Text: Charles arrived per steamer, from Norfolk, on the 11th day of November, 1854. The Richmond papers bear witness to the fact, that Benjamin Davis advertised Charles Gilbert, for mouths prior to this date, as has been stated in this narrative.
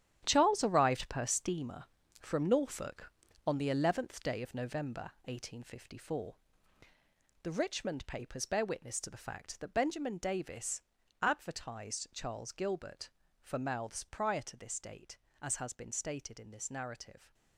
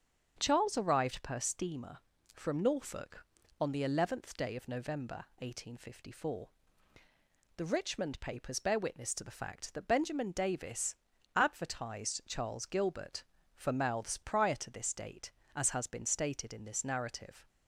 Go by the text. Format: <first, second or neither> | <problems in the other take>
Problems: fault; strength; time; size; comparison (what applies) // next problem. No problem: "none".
second | gets quieter; strong; throughout; 11 dB // starts louder than the rest; strong; until 1.2 s; 11 dB; strong in the second // pauses between "Davis" and "advertised"; at 10.7 s; 0.42 s long; also in the second